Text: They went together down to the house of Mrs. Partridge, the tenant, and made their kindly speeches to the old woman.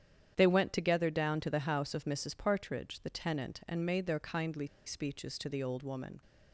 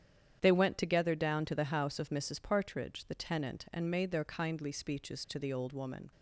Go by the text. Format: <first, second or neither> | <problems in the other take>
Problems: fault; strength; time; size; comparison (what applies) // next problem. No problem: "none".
second | starts louder than the rest; strong; until 1.3 s; 9 dB; strong in the second // pauses between "kindly" and "speeches"; slight; at 4.6 s; 0.19 s long